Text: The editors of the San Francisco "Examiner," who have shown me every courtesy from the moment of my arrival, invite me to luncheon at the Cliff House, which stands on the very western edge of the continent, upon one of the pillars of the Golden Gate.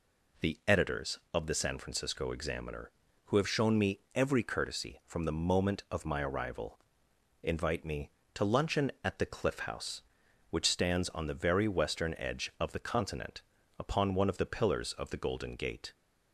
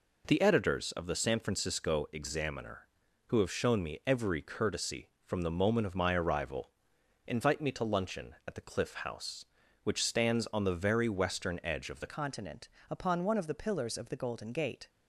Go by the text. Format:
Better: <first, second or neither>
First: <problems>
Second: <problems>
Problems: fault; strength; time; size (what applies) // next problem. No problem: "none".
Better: first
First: none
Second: changes voice at "continent"; from 12.0 s on; 2.8 s long